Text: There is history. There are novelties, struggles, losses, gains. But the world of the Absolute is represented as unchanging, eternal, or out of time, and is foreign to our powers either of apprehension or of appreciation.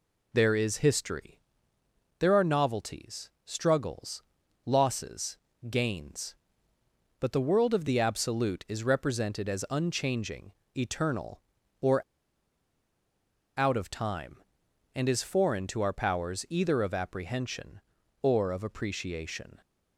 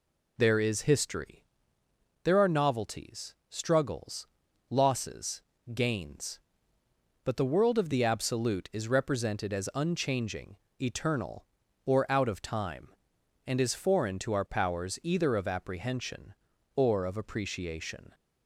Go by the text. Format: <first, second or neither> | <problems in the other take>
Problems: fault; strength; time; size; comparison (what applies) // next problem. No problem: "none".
second | pauses between "or" and "out"; strong; at 12.0 s; 1.5 s long